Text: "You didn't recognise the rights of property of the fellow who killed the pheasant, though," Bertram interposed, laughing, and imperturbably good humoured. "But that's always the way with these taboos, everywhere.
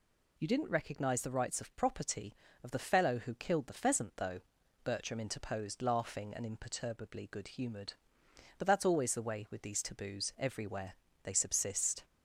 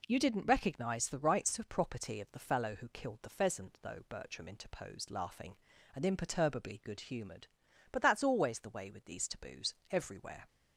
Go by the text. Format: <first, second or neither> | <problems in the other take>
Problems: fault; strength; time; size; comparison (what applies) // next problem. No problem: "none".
second | goes on to say "They subsist"; noticeable; from 11.2 s on; 0.82 s long